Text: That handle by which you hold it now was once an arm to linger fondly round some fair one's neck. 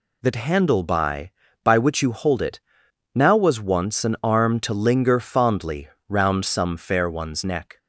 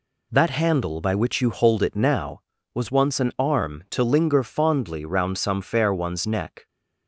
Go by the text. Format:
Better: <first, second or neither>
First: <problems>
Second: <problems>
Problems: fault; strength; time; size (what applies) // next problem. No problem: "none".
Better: second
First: says "by" twice; at 1.6 s // pauses between "it" and "now"; noticeable; at 2.6 s; 0.54 s long // pauses between "fondly" and "round"; slight; at 5.8 s; 0.20 s long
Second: none